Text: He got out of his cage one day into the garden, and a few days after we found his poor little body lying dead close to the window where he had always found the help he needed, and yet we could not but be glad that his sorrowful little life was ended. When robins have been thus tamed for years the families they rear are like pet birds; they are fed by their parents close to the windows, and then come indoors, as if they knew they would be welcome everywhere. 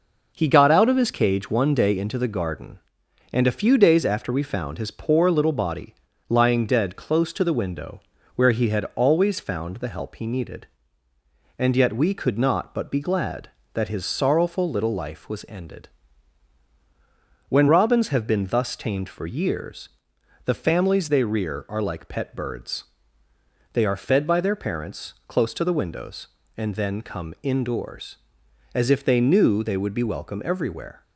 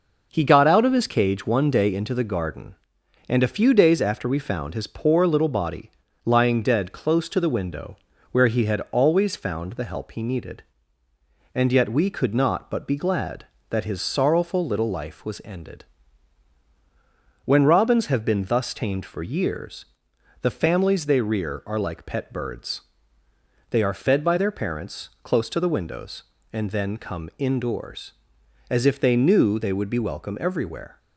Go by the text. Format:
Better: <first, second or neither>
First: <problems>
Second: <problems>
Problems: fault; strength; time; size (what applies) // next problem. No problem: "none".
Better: neither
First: pauses between "body" and "lying"; slight; at 5.9 s; 0.34 s long // pauses between "window" and "where"; slight; at 8.0 s; 0.34 s long // pauses between "years" and "the"; noticeable; at 19.8 s; 0.56 s long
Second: pauses between "body" and "lying"; slight; at 5.8 s; 0.34 s long // pauses between "window" and "where"; slight; at 7.9 s; 0.34 s long // pauses between "years" and "the"; noticeable; at 19.8 s; 0.56 s long